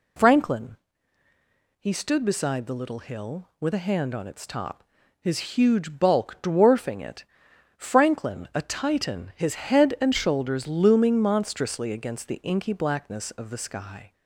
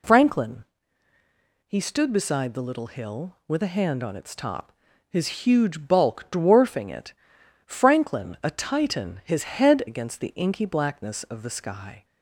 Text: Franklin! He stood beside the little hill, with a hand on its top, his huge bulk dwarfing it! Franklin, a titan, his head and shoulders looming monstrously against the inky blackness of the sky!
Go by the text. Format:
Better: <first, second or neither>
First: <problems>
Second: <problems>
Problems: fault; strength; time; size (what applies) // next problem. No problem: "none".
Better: first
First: none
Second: skips "and shoulders looming monstrously"; at 9.8 s